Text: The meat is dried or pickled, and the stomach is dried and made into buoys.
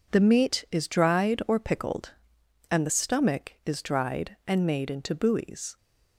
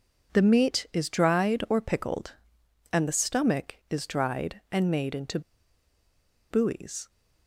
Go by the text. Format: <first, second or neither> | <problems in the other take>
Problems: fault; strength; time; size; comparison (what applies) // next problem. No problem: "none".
first | pauses between "into" and "buoys"; at 5.3 s; 1.1 s long